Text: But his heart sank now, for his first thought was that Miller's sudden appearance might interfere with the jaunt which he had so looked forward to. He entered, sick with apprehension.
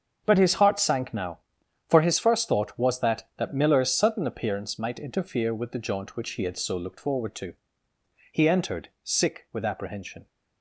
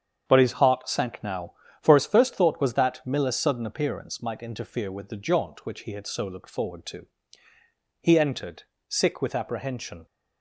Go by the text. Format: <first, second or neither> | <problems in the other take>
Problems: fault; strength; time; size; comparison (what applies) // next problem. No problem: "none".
second | starts louder than the rest; until 1.2 s; 7 dB; strong in the second // says "that" twice; at 3.3 s